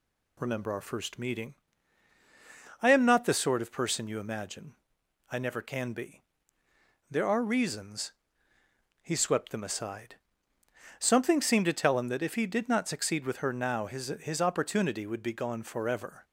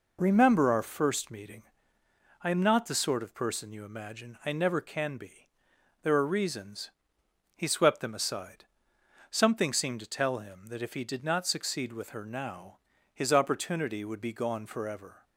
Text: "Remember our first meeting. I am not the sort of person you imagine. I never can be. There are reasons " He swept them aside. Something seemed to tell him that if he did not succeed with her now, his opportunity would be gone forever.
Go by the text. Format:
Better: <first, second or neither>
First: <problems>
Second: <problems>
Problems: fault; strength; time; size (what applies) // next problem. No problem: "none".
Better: second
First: says "his" twice; at 14.2 s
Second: none